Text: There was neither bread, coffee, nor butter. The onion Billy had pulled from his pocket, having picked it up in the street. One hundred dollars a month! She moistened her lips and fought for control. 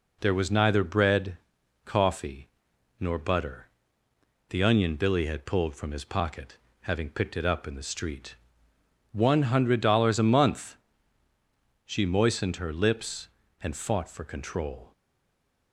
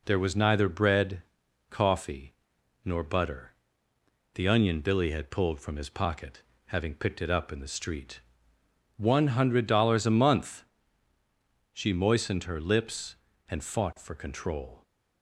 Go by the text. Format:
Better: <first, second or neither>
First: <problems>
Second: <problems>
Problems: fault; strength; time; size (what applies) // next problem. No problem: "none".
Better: second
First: stays silent after the last word; slight; from 14.9 s on; 0.8 s long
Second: none